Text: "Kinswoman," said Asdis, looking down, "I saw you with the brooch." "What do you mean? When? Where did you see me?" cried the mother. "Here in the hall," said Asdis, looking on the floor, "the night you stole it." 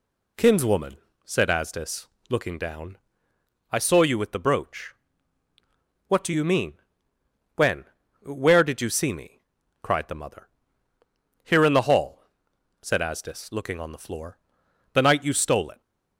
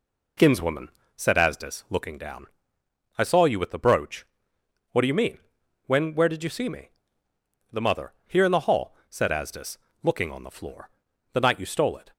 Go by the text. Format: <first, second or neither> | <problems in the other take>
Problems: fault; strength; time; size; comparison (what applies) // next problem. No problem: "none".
first | skips "cried"; at 7.3 s